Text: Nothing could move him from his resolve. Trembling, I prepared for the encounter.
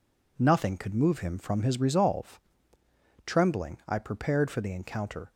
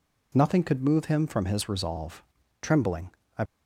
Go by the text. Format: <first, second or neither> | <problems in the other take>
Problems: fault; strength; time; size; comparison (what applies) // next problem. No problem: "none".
first | stops before "prepared for the encounter"; at 3.4 s